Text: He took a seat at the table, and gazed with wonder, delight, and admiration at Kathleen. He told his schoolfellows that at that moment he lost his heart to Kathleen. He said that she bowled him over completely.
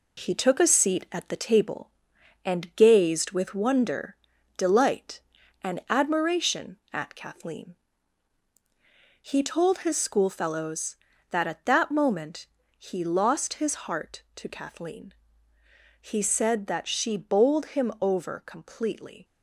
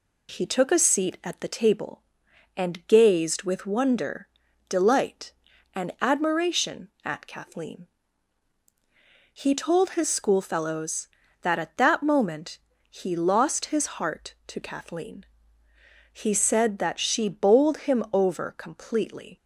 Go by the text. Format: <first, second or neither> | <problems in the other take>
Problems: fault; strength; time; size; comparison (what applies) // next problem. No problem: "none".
second | gets quieter; noticeable; throughout; 4.5 dB // pauses between "moment" and "he"; slight; at 12.4 s; 0.30 s long; slight in the second